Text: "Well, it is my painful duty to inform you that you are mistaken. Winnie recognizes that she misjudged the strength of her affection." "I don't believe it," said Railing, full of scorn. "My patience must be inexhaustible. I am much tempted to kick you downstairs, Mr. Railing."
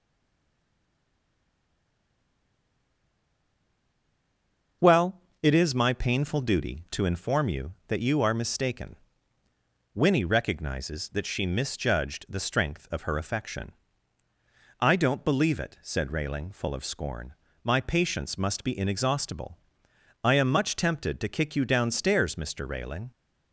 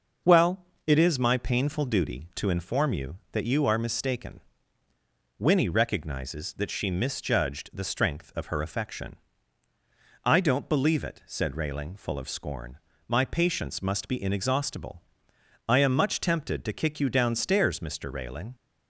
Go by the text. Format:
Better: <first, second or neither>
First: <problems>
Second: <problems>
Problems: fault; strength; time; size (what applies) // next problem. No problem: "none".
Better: second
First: stays silent before the first word; strong; until 4.8 s; 4.8 s long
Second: none